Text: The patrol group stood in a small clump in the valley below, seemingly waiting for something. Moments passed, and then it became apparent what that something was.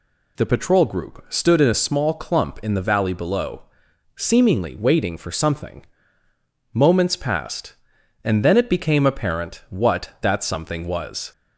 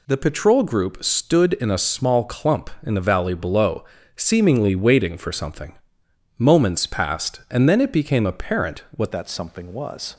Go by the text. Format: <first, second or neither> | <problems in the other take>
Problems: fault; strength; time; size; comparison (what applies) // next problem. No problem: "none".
first | changes voice at "that"; from 9.1 s on; 1.0 s long